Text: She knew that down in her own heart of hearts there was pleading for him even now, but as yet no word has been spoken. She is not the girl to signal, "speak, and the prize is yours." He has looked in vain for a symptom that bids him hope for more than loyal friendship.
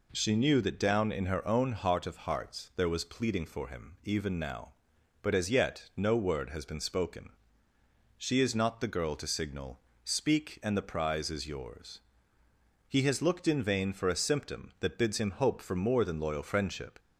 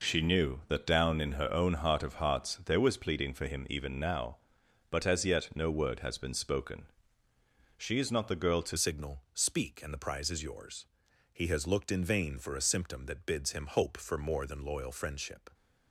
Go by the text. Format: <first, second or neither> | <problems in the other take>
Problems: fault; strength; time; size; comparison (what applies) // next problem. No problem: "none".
first | changes voice at "signal"; from 8.7 s on; 6.7 s long